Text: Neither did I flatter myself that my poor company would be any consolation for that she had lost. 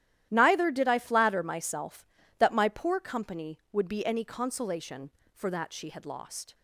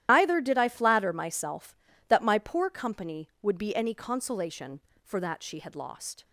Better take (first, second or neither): first